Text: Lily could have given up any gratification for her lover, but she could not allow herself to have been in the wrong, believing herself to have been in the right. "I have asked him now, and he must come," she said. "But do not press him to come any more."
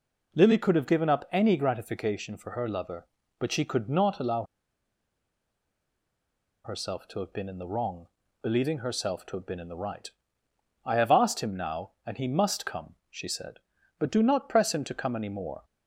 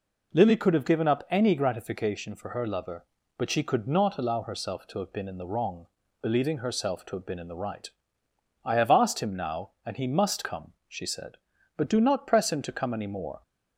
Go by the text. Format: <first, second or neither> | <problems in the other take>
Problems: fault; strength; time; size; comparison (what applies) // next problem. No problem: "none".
second | pauses between "allow" and "herself"; strong; at 4.4 s; 2.2 s long